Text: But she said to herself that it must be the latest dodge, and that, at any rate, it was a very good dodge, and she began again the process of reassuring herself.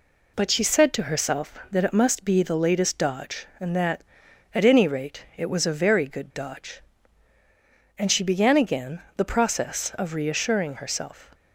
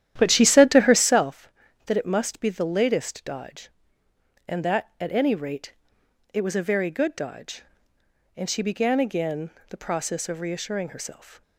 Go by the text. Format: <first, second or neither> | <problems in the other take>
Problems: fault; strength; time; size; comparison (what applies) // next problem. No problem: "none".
first | starts louder than the rest; strong; until 1.3 s; 11 dB // pauses between "again" and "the"; slight; at 9.4 s; 0.20 s long